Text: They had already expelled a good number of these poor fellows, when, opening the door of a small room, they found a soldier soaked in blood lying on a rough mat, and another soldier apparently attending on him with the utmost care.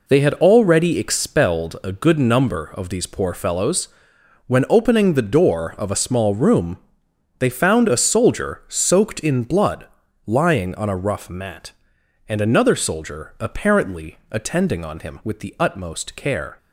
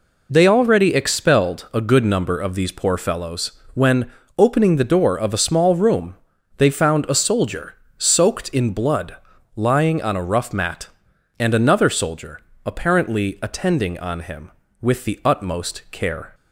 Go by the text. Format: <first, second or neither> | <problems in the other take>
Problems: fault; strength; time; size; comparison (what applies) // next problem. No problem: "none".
first | skips "had"; at 0.4 s // pauses between "soldier" and "soaked"; slight; at 7.7 s; 0.24 s long // pauses between "blood" and "lying"; at 9.1 s; 0.40 s long; also in the first // pauses between "soldier" and "apparently"; slight; at 12.4 s; 0.24 s long